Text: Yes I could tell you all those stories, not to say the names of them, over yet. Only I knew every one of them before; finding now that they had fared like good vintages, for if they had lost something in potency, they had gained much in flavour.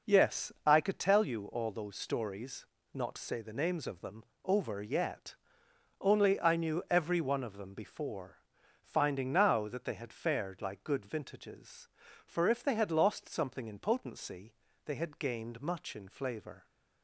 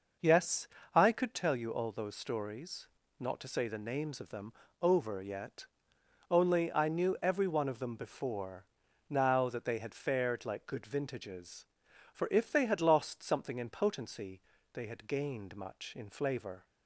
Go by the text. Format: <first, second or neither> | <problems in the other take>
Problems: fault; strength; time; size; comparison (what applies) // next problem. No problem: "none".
first | pauses between "Yes" and "I"; slight; at 0.6 s; 0.28 s long; slight in the first // skips "finding"; at 8.8 s